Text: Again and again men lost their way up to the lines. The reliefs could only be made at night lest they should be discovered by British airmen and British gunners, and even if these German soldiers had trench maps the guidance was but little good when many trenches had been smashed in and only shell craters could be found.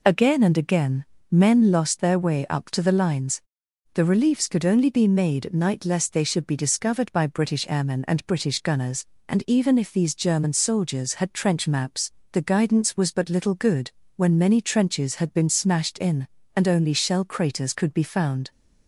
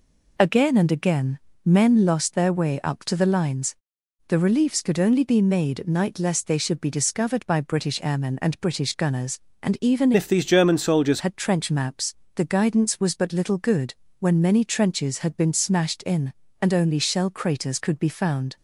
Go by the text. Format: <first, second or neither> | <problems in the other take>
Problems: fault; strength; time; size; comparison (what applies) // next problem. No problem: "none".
first | pauses between "again" and "men"; slight; at 1.3 s; 0.26 s long; slight in the first // changes voice from "if" to "soldiers"; from 10.1 to 11.2 s; 1.1 s long // pauses between "maps" and "the"; slight; at 12.1 s; 0.22 s long; slight in the first // pauses between "good" and "when"; slight; at 13.9 s; 0.26 s long; slight in the first